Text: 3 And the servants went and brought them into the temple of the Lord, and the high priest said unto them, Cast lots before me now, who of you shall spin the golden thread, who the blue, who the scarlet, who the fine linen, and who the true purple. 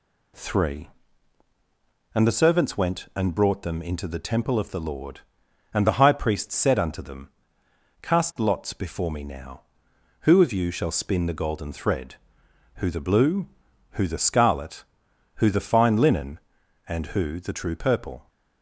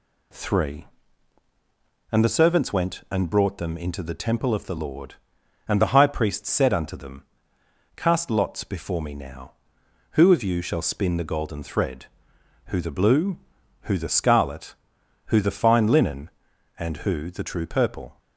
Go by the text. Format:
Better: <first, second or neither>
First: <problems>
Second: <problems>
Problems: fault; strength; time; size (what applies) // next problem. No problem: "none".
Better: neither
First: none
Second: none